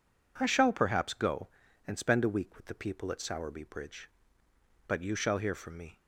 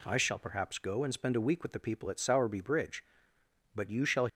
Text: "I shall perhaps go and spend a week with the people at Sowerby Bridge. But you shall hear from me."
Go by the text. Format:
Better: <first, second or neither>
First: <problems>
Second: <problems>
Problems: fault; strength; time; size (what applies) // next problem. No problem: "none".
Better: first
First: none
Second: stops before "hear from me"; at 4.2 s